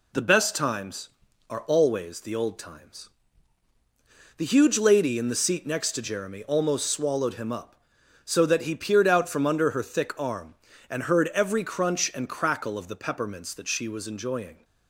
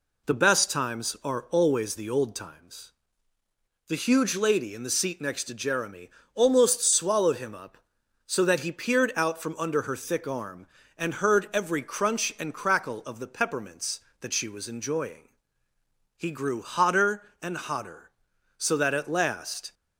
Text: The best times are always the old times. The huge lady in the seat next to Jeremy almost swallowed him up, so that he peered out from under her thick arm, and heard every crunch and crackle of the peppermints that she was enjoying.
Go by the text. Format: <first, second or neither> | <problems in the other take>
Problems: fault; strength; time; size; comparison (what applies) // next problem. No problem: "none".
first | pauses between "Jeremy" and "almost"; slight; at 6.0 s; 0.24 s long // goes on to say "He grew hotter and hotter so that at last"; strong; from 16.1 s on; 3.5 s long